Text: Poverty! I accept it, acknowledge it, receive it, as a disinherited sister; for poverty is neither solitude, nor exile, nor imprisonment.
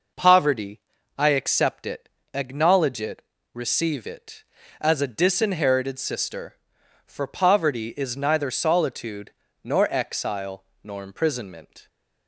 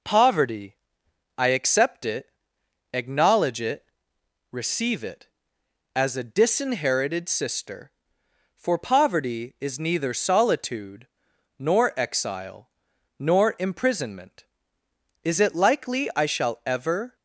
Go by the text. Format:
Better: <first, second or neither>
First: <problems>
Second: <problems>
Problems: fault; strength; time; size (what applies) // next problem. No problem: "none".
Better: first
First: none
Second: goes on to say "Is it likely I shall ever"; strong; from 15.2 s on; 1.9 s long